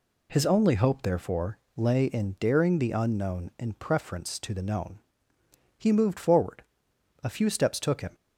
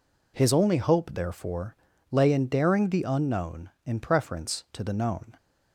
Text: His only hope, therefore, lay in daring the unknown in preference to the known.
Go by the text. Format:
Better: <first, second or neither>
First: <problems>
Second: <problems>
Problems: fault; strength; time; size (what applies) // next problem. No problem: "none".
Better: second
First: goes on to say "He moved forward A few steps took him"; strong; from 5.7 s on; 2.3 s long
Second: none